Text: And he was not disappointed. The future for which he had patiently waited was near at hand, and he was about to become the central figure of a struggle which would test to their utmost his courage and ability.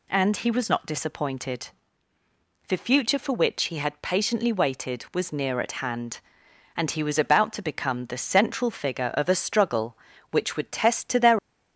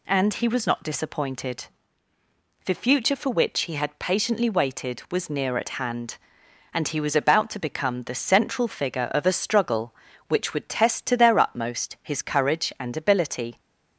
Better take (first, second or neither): second